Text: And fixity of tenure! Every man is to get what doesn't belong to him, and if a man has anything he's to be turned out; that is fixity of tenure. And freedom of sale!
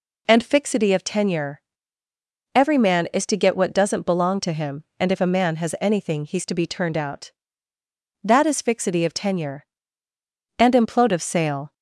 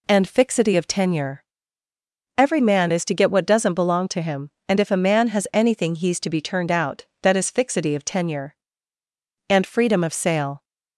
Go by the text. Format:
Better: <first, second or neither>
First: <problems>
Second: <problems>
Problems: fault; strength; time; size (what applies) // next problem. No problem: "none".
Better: second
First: says "implode" for "freedom"; at 10.7 s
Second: none